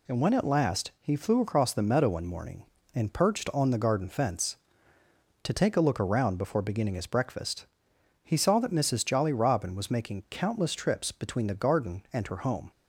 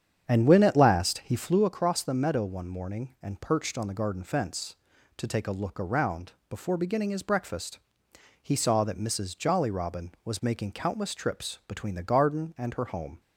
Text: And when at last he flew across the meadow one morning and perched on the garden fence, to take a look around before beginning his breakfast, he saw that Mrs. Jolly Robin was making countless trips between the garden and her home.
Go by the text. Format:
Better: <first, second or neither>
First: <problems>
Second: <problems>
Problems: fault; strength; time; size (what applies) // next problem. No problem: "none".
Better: first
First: none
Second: starts louder than the rest; strong; until 1.7 s; 8 dB // pauses between "around" and "before"; slight; at 6.3 s; 0.18 s long